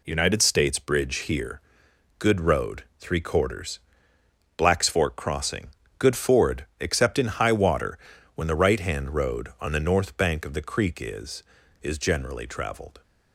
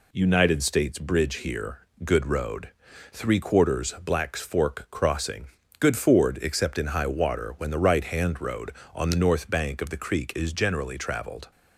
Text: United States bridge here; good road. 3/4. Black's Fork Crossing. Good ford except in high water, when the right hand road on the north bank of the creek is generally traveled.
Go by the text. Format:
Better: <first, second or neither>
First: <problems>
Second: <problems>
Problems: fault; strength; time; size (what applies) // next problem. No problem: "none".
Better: second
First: pauses between "ford" and "except"; slight; at 6.6 s; 0.16 s long // says "is" twice; at 11.8 s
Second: none